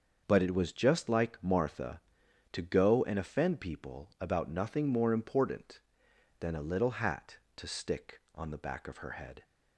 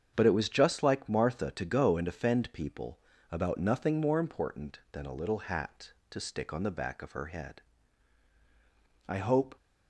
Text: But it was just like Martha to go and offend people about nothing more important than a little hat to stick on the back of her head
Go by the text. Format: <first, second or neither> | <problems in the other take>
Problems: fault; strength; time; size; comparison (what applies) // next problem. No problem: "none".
first | starts louder than the rest; strong; until 1.1 s; 7.5 dB; also in the first // pauses between "people" and "about"; slight; at 2.9 s; 0.32 s long // goes on to say "I hope"; slight; from 9.0 s on; 0.48 s long